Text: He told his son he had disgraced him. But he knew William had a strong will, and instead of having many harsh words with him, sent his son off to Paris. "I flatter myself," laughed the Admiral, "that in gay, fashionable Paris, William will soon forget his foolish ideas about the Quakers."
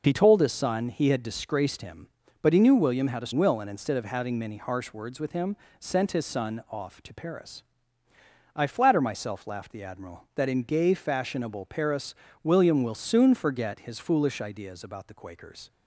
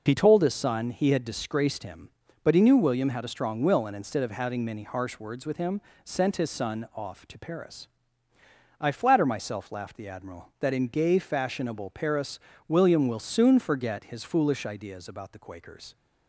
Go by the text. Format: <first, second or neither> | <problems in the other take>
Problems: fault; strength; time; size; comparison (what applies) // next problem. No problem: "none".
second | skips "strong"; at 3.3 s